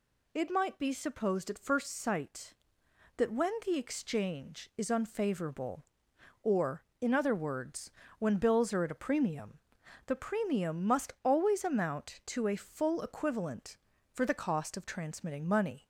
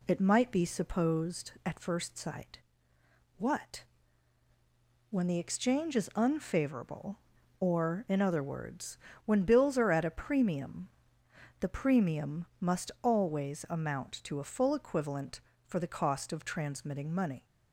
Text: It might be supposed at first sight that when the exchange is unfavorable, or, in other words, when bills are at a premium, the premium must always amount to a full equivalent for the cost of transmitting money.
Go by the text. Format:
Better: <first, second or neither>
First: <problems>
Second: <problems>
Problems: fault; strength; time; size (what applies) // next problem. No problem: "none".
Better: first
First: none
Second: says "what" for "that"; at 3.3 s